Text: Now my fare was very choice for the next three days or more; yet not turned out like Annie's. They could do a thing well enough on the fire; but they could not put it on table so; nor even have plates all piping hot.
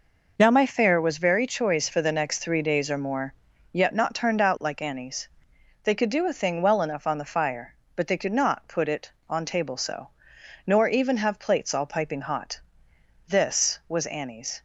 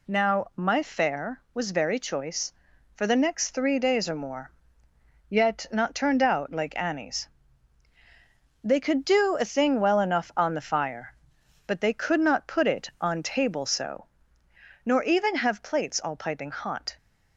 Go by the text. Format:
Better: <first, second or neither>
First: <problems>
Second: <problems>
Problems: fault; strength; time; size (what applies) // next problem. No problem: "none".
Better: second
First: goes on to say "This was Annie's"; from 13.2 s on; 1.3 s long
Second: none